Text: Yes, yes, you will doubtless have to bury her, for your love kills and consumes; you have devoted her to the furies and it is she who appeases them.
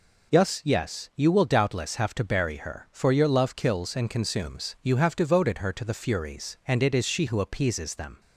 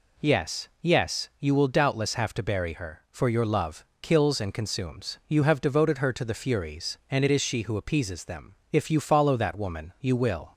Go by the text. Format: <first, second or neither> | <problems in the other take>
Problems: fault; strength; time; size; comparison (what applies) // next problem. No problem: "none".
first | pauses between "love" and "kills"; slight; at 3.8 s; 0.18 s long // goes on to say "If you follow that woman you will"; strong; from 8.7 s on; 1.8 s long